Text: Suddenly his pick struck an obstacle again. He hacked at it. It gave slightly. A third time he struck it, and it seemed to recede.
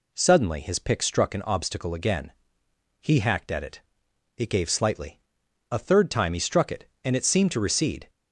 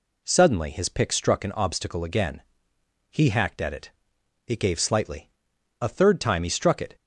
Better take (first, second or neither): first